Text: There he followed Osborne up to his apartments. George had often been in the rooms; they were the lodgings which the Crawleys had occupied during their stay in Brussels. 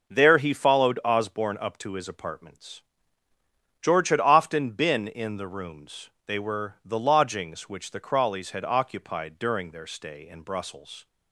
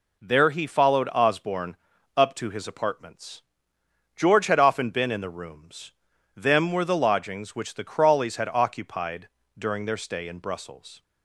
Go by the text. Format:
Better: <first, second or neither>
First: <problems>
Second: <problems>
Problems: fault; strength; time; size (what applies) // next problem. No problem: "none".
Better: first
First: none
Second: pauses between "Osborne" and "up"; at 1.7 s; 0.40 s long // says "them" for "they"; at 6.3 s // pauses between "occupied" and "during"; slight; at 9.2 s; 0.28 s long